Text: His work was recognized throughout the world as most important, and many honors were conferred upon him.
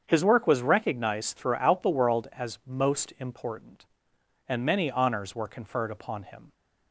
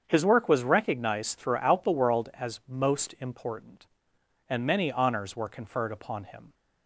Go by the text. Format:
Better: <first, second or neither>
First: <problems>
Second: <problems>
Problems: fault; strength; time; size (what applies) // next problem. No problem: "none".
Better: neither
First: starts louder than the rest; strong; until 1.0 s; 7.5 dB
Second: starts louder than the rest; strong; until 1.0 s; 7.5 dB